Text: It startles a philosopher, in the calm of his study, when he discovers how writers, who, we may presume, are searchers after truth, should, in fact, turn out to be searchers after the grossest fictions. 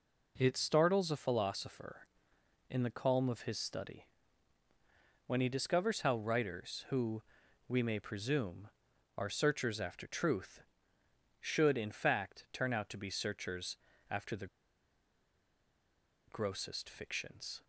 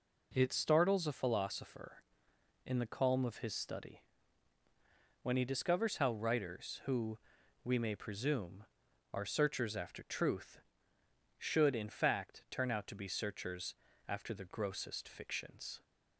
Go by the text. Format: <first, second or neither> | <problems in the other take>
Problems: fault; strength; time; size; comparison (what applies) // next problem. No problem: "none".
second | pauses between "searchers" and "after"; slight; at 13.7 s; 0.32 s long; slight in the second // pauses between "the" and "grossest"; strong; at 14.4 s; 1.8 s long